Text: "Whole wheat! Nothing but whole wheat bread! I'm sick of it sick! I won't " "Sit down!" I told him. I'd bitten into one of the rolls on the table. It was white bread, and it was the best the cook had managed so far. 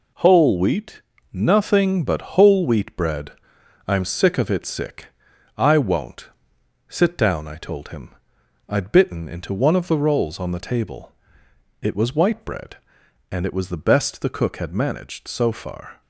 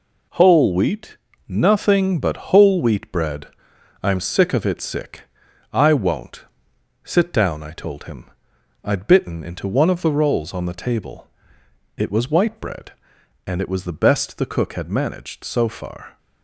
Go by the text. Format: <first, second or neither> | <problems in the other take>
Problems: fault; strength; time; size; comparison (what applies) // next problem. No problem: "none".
neither | none